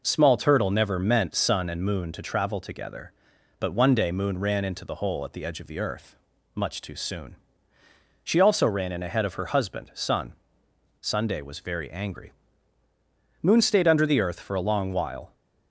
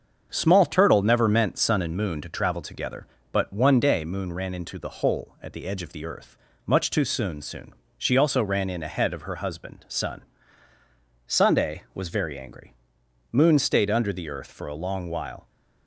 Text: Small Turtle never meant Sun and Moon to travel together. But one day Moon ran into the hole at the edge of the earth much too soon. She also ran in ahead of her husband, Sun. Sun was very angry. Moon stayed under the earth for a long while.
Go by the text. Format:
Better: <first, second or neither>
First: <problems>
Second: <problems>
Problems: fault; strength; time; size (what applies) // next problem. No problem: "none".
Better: first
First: pauses between "earth" and "much"; at 6.1 s; 0.38 s long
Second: starts louder than the rest; until 1.3 s; 7 dB // pauses between "earth" and "much"; slight; at 6.3 s; 0.30 s long // says "soon" twice; at 7.4 s